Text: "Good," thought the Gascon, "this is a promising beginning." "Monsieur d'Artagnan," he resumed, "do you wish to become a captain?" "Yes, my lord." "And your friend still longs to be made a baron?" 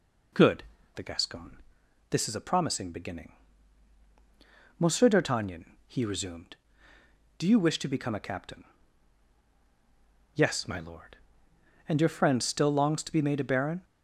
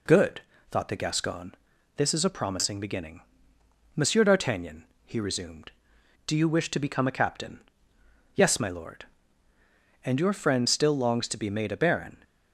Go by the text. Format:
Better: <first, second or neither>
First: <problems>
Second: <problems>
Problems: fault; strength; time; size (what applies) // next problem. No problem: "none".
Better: second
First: skips "thought"; at 0.7 s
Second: none